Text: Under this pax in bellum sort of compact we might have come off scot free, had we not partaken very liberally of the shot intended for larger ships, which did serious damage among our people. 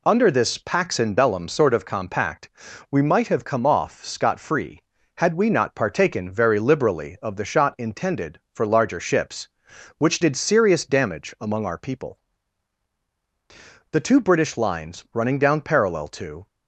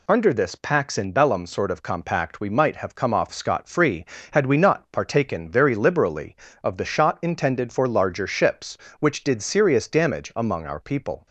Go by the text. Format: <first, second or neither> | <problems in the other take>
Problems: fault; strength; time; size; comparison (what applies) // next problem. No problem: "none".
second | pauses between "compact" and "we"; at 2.4 s; 0.42 s long // goes on to say "The two British lines running down parallel to"; strong; from 13.9 s on; 2.5 s long